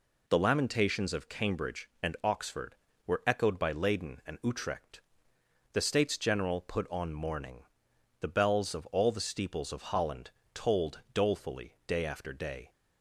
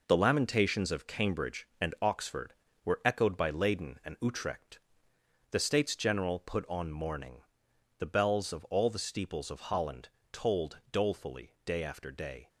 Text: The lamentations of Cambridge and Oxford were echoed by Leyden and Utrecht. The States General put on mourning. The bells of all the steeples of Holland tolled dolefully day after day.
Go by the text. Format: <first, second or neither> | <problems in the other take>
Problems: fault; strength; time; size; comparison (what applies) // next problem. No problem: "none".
first | gets quieter; strong; throughout; 7.5 dB // pauses between "Holland" and "tolled"; slight; at 10.0 s; 0.22 s long; slight in the first